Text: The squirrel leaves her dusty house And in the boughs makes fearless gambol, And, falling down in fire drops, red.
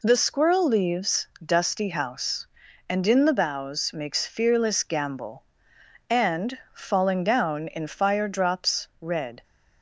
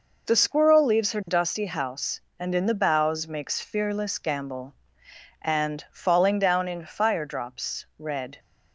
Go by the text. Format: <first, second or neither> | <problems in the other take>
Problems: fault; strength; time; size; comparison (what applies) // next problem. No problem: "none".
second | skips "her"; at 1.3 s